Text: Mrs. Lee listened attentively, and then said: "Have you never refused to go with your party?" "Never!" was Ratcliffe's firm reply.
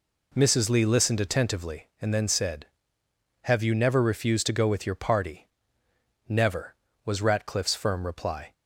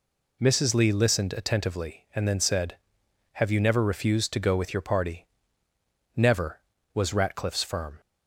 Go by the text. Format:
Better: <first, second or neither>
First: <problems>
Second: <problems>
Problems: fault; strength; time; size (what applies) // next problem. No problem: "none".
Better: first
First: none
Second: stops before "reply"; at 8.0 s